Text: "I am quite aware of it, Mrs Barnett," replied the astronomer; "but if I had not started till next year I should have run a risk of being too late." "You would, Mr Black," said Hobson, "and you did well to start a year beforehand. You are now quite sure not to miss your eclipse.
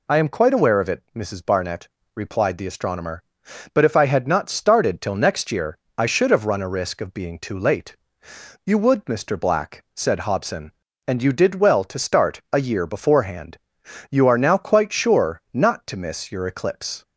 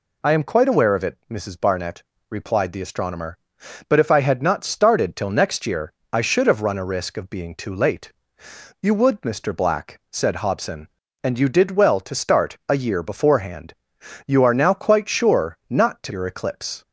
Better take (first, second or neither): first